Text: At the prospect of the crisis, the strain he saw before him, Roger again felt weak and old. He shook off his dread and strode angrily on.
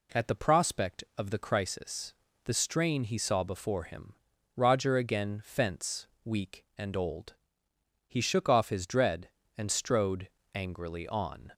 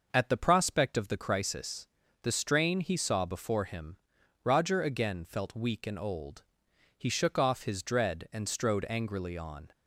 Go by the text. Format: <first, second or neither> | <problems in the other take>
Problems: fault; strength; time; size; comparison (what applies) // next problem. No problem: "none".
second | says "fence" for "felt"; at 5.4 s // pauses between "strode" and "angrily"; slight; at 10.2 s; 0.24 s long